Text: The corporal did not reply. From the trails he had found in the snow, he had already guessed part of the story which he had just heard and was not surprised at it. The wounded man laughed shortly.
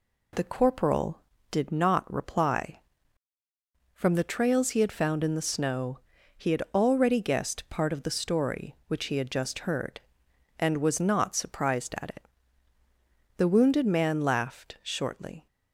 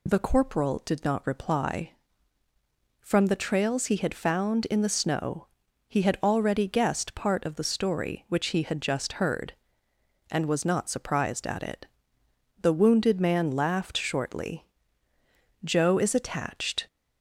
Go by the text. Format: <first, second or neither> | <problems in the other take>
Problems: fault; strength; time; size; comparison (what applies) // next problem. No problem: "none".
first | goes on to say "Joe is attached"; noticeable; from 15.6 s on; 1.2 s long